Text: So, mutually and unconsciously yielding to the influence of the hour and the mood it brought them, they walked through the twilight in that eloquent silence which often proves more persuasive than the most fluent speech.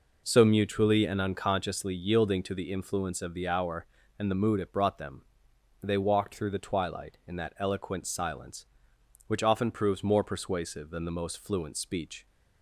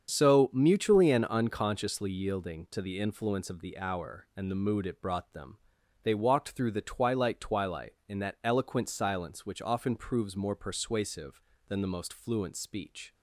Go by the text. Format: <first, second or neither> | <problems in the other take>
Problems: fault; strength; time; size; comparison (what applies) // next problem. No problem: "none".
first | starts louder than the rest; strong; until 1.1 s; 7.5 dB // says "twilight" twice; at 7.3 s